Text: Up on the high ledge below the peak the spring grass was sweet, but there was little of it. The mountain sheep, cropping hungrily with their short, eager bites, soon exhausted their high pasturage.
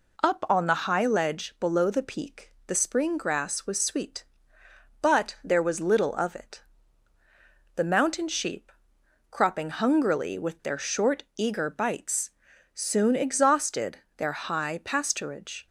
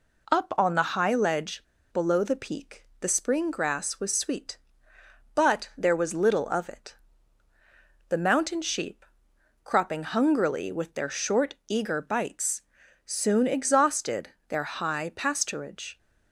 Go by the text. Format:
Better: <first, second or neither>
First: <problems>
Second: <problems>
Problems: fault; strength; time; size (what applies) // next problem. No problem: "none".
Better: first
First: pauses between "exhausted" and "their"; slight; at 13.9 s; 0.18 s long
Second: pauses between "ledge" and "below"; slight; at 1.6 s; 0.31 s long // pauses between "exhausted" and "their"; slight; at 14.2 s; 0.18 s long